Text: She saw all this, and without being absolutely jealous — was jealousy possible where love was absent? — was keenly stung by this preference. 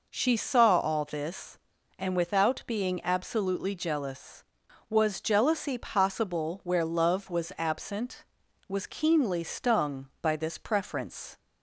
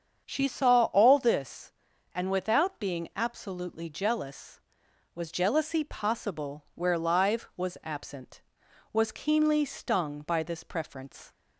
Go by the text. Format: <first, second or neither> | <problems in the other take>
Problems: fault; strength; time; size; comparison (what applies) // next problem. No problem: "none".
first | starts louder than the rest; strong; until 1.2 s; 7.5 dB // says "live" for "love"; at 6.9 s